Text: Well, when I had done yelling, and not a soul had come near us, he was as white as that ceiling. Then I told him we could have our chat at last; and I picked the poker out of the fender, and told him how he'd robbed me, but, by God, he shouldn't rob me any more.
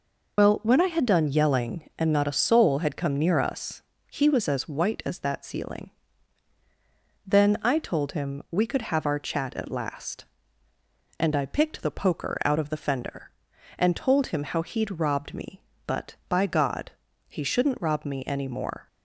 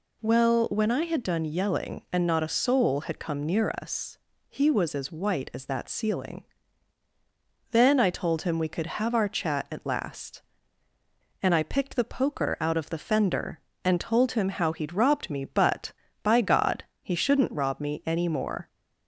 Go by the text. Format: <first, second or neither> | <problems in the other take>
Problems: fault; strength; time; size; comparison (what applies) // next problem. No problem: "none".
second | loses the start of "Well"; at 0.3 s; 50 ms